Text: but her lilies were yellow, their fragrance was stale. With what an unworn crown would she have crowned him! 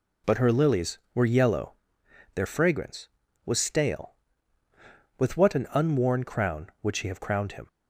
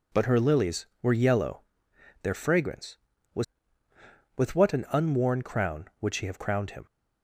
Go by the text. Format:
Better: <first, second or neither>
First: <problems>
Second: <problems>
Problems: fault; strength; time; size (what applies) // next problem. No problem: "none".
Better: first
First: none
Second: skips "stale"; at 3.9 s